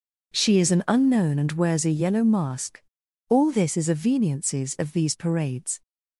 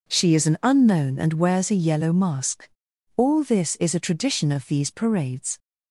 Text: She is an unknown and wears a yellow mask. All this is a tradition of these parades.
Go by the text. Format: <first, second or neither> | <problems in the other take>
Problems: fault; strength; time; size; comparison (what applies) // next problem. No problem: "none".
second | says "veniences" for "tradition"; at 3.9 s